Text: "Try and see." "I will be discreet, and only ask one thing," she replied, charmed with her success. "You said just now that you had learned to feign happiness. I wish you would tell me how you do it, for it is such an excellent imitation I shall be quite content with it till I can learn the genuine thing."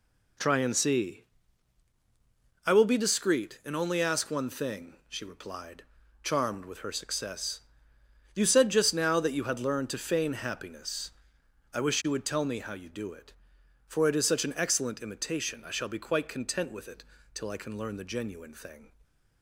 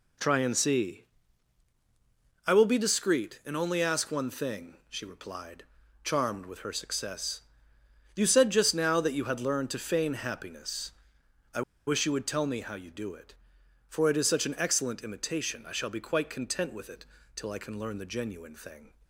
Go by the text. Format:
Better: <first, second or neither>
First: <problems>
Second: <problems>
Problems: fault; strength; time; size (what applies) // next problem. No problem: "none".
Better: first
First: pauses between "it" and "till"; slight; at 17.0 s; 0.32 s long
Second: pauses between "I" and "wish"; slight; at 11.6 s; 0.26 s long // pauses between "it" and "till"; slight; at 17.0 s; 0.32 s long